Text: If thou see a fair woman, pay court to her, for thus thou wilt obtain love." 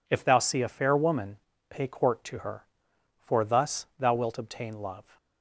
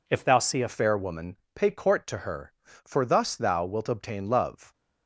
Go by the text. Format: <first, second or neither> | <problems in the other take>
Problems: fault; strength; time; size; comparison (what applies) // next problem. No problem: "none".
first | changes voice at "fair"; from 0.6 s on; 4.1 s long